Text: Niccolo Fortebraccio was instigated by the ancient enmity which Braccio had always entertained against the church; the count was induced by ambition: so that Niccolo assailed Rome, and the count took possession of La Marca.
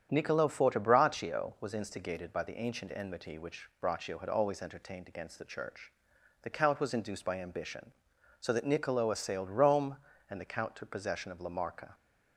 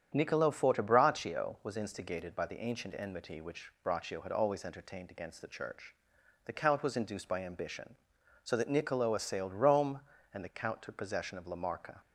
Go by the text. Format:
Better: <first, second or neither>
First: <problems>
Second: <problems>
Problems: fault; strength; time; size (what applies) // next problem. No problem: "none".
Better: neither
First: starts louder than the rest; strong; until 1.1 s; 8.5 dB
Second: starts louder than the rest; strong; until 1.1 s; 8.5 dB